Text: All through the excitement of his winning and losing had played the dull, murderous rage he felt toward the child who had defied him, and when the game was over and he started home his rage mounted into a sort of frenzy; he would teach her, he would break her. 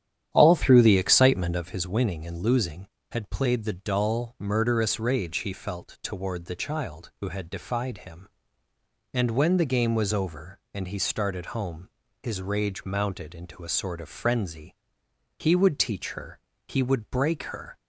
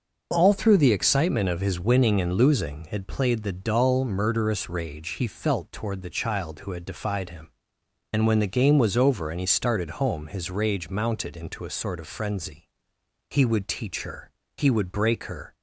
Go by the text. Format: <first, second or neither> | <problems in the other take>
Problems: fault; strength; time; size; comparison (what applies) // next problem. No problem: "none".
second | starts louder than the rest; strong; until 1.7 s; 10 dB // pauses between "home" and "his"; slight; at 11.8 s; 0.32 s long